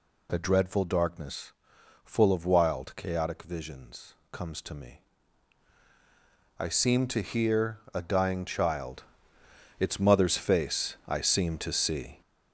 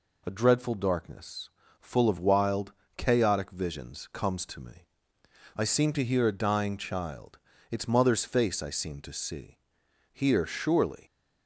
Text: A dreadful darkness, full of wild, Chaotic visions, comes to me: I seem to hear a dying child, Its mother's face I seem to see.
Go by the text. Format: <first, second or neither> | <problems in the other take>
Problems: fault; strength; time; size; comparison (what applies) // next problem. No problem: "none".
first | goes on to say "Here surely"; noticeable; from 10.1 s on; 0.94 s long